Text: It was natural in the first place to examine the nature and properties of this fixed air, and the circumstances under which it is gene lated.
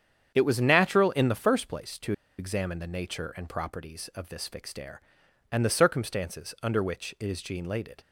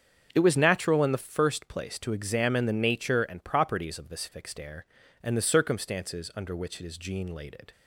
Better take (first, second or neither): second